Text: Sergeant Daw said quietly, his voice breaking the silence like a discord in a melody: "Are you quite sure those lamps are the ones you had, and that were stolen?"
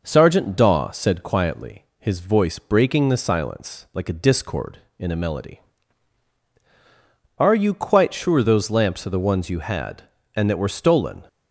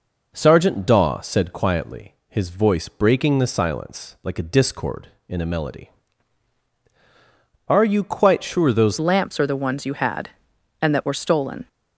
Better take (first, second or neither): first